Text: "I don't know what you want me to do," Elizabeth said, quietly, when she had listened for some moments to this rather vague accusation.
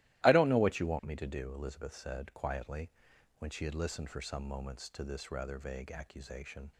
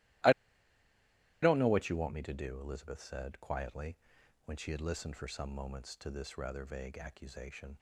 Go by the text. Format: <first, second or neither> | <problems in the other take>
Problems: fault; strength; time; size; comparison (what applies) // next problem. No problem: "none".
first | starts louder than the rest; strong; until 2.3 s; 15.5 dB; strong in the first // pauses between "I" and "don't"; at 0.3 s; 1.1 s long